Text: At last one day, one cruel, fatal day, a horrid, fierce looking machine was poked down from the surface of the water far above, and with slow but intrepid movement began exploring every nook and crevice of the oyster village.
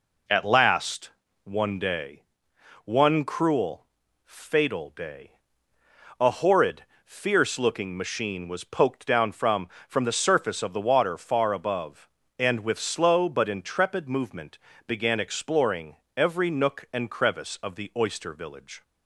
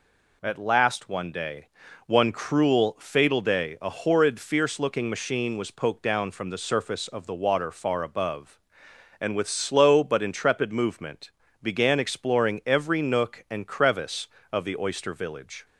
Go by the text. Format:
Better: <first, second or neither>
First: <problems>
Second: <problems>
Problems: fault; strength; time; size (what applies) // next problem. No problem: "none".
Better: second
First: pauses between "last" and "one"; slight; at 1.1 s; 0.34 s long // says "from" twice; at 9.8 s // pauses between "movement" and "began"; slight; at 14.5 s; 0.30 s long // pauses between "exploring" and "every"; slight; at 15.9 s; 0.22 s long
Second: pauses between "movement" and "began"; slight; at 11.3 s; 0.30 s long